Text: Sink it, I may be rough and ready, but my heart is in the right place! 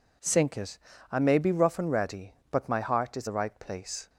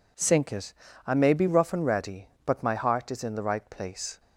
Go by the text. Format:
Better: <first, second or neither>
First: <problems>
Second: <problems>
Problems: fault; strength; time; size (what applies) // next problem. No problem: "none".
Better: second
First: skips "in"; at 3.2 s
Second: none